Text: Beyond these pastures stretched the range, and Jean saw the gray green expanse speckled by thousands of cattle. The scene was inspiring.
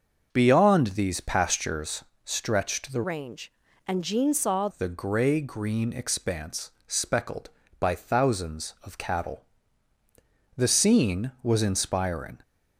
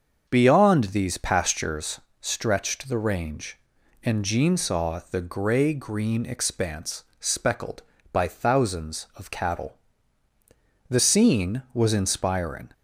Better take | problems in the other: second | starts louder than the rest; until 1.3 s; 6.5 dB; also in the second // pauses between "pastures" and "stretched"; slight; at 2.0 s; 0.20 s long; slight in the second // changes voice from "range" to "saw"; from 3.0 to 4.6 s; 1.6 s long // pauses between "expanse" and "speckled"; slight; at 6.7 s; 0.16 s long; slight in the second

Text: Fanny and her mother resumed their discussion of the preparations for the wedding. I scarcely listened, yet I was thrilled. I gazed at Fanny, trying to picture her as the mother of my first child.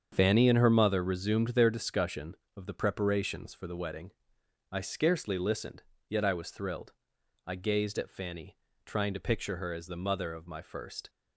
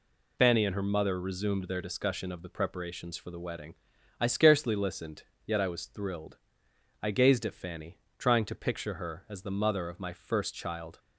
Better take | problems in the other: second | starts louder than the rest; strong; until 1.1 s; 7.5 dB // stops before "child"; at 11.0 s

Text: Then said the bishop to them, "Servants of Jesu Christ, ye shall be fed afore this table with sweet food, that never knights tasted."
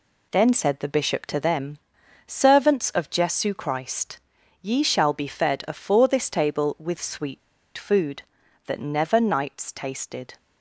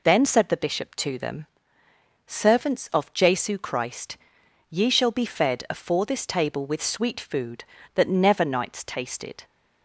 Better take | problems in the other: second | pauses between "sweet" and "food"; at 7.3 s; 0.36 s long

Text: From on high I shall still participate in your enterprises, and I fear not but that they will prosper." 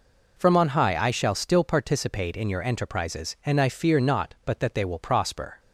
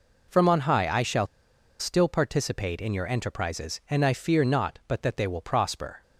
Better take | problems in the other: first | pauses between "shall" and "still"; noticeable; at 1.2 s; 0.54 s long

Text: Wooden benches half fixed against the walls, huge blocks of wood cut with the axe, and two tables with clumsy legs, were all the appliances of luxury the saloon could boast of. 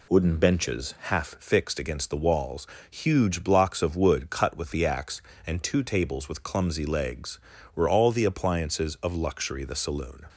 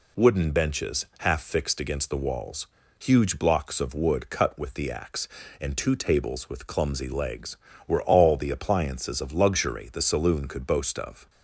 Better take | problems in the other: second | stops before "could boast of"; at 10.2 s

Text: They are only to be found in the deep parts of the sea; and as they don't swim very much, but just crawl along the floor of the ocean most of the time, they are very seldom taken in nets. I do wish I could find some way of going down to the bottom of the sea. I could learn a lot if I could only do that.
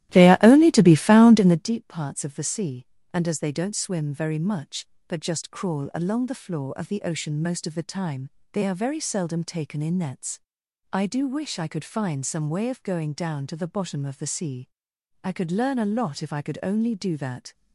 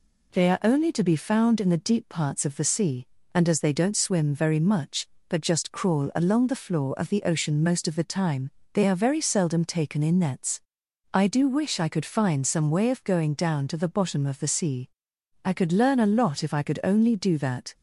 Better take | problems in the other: second | starts louder than the rest; strong; until 1.7 s; 14.5 dB

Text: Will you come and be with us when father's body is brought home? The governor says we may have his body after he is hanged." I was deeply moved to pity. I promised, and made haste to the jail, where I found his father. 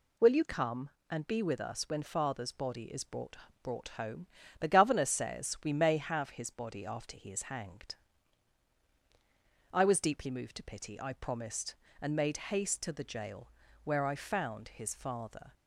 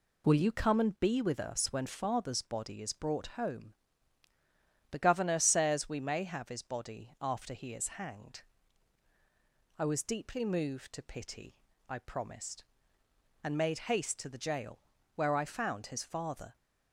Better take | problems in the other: second | says "brought" twice; at 3.6 s

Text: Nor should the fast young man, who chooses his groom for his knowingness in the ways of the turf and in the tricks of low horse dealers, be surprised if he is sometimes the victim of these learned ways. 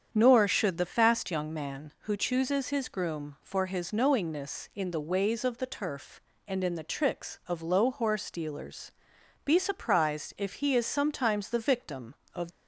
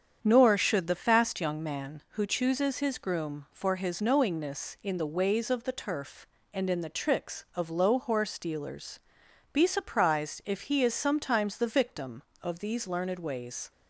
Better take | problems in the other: second | starts louder than the rest; strong; until 1.1 s; 8 dB; strong in the second // stops before "these learned ways"; at 12.5 s

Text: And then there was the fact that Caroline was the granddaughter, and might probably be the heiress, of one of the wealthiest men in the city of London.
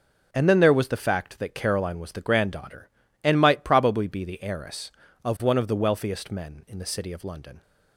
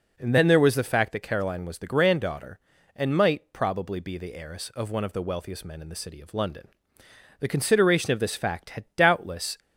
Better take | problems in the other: first | goes on to say "The consideration of this fact had doubtless"; strong; from 7.4 s on; 2.1 s long

